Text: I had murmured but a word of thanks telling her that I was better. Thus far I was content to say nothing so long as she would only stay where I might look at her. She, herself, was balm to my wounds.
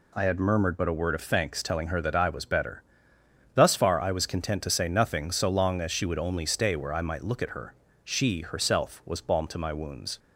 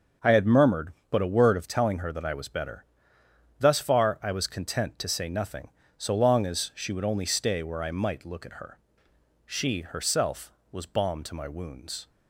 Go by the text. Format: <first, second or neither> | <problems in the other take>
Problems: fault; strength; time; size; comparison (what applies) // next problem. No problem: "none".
first | starts louder than the rest; until 1.4 s; 6.5 dB // skips "thanks"; at 1.6 s